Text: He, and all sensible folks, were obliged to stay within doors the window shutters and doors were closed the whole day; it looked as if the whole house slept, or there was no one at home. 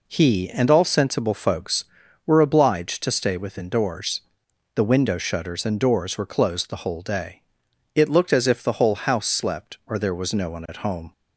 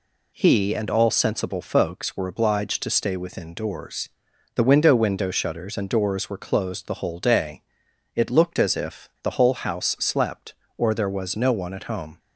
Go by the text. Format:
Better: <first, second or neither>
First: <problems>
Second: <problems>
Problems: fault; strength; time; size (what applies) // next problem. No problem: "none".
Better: first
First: pauses between "doors" and "the"; noticeable; at 4.2 s; 0.52 s long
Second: pauses between "doors" and "the"; noticeable; at 4.0 s; 0.46 s long // says "window" twice; at 4.9 s